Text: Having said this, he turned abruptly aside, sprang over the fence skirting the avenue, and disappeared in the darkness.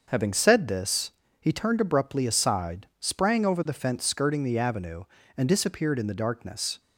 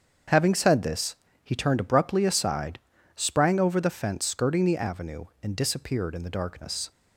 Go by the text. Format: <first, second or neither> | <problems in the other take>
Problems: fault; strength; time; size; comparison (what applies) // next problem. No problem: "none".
neither | starts louder than the rest; the same in both